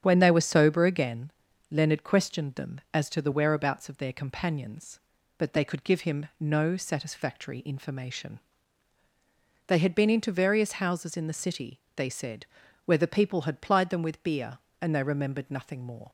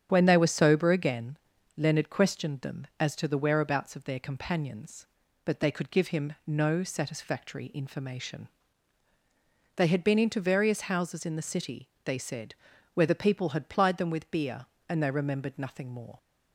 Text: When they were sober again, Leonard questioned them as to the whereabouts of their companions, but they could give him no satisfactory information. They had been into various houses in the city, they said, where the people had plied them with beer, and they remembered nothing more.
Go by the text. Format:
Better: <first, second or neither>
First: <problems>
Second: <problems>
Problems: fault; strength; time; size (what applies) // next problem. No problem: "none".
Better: neither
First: starts louder than the rest; strong; until 1.0 s; 9 dB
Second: starts louder than the rest; strong; until 1.1 s; 9 dB